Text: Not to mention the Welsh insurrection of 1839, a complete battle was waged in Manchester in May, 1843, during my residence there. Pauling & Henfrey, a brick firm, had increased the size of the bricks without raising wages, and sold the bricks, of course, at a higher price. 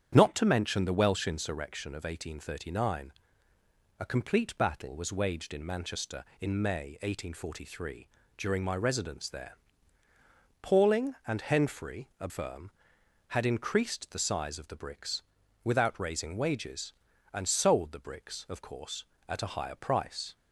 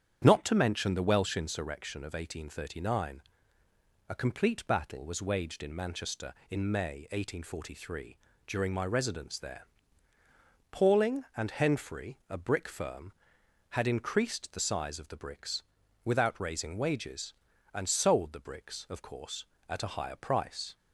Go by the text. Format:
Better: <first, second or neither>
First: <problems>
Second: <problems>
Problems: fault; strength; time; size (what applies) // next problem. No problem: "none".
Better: second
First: starts louder than the rest; strong; until 1.1 s; 9 dB // skips "brick"; at 12.2 s // pauses between "bricks" and "without"; at 15.2 s; 0.40 s long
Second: starts louder than the rest; strong; until 1.2 s; 9 dB // pauses between "bricks" and "without"; at 15.6 s; 0.40 s long